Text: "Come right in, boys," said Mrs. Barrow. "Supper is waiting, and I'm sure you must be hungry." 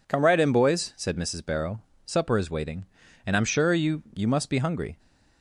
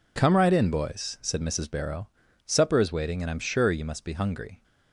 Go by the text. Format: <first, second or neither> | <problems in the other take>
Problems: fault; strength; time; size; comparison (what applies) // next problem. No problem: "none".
second | says "you" twice; at 4.1 s